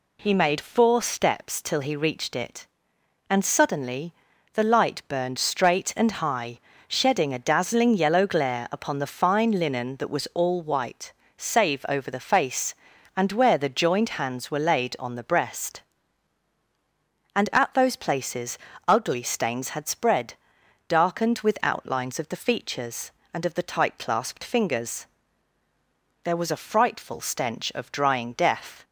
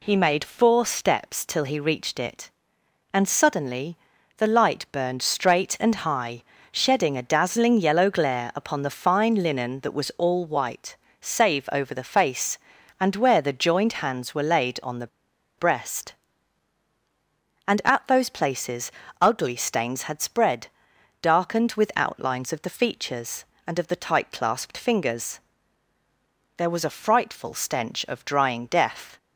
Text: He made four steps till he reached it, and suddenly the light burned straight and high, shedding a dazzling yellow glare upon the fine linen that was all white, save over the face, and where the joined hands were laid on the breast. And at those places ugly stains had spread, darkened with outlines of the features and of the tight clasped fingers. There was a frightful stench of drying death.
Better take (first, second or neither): first